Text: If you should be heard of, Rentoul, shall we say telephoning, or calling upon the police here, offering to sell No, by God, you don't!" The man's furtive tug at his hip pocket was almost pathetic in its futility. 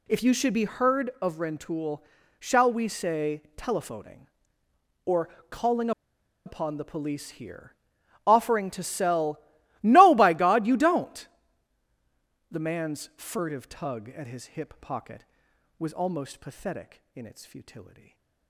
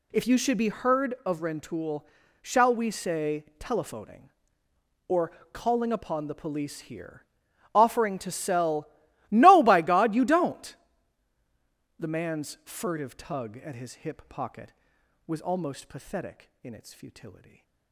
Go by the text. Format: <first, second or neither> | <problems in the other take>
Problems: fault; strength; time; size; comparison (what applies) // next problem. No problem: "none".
second | pauses between "or" and "calling"; slight; at 5.2 s; 0.22 s long; slight in the second // pauses between "calling" and "upon"; noticeable; at 5.9 s; 0.55 s long // pauses between "sell" and "No"; at 9.3 s; 0.44 s long; also in the second // stays silent after the last word; slight; from 17.8 s on; 0.6 s long; slight in the second